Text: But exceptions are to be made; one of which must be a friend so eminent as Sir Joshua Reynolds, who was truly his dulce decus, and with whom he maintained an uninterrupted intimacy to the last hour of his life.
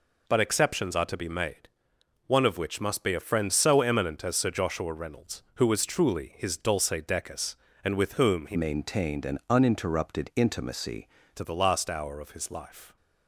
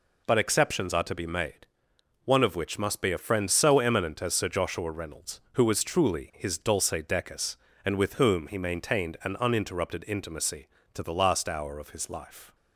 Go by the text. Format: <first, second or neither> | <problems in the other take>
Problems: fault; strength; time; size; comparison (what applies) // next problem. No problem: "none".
second | changes voice from "maintained" to "intimacy"; from 8.5 to 11.0 s; 2.5 s long